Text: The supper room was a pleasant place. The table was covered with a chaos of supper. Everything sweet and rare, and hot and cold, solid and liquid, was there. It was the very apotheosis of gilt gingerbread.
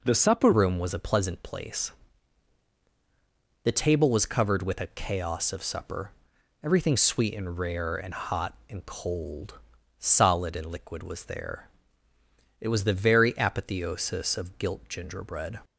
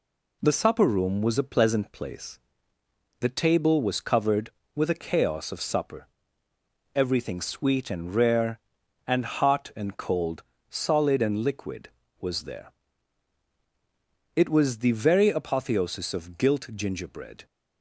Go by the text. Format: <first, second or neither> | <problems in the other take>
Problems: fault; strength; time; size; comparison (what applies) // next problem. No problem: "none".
second | changes voice at "room"; from 0.5 s on; 15.0 s long